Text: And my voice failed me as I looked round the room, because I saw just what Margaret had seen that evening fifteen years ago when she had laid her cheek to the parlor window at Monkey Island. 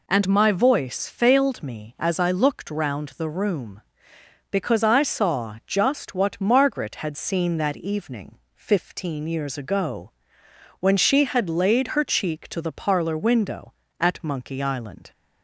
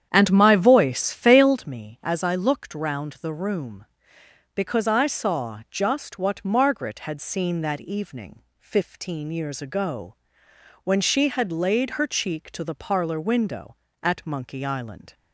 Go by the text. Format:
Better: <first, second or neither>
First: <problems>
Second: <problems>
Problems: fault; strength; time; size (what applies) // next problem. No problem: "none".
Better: first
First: pauses between "evening" and "fifteen"; slight; at 8.3 s; 0.18 s long // pauses between "ago" and "when"; noticeable; at 10.1 s; 0.68 s long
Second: starts louder than the rest; strong; until 1.7 s; 9 dB // pauses between "evening" and "fifteen"; slight; at 8.4 s; 0.18 s long // pauses between "ago" and "when"; noticeable; at 10.1 s; 0.68 s long